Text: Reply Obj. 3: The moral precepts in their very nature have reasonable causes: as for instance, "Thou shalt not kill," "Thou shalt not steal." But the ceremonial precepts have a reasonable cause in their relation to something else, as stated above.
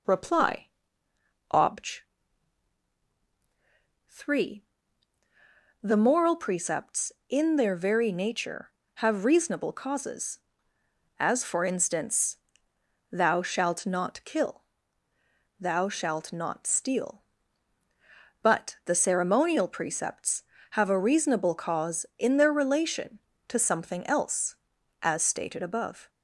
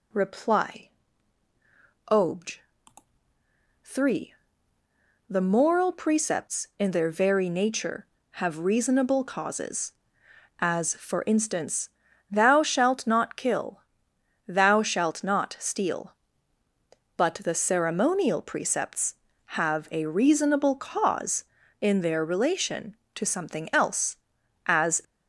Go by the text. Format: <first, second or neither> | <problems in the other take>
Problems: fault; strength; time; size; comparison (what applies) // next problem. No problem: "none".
first | pauses between "Reply" and "Obj"; at 0.8 s; 1.2 s long; noticeable in the first // stops before "stated above"; at 25.0 s